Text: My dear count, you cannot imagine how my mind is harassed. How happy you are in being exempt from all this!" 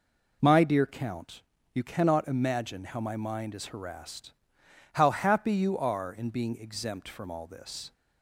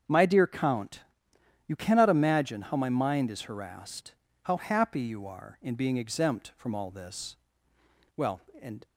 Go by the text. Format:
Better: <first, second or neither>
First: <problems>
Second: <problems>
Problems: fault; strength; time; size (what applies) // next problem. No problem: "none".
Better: first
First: none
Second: starts louder than the rest; strong; until 1.7 s; 7 dB // goes on to say "Well and"; noticeable; from 8.1 s on; 0.70 s long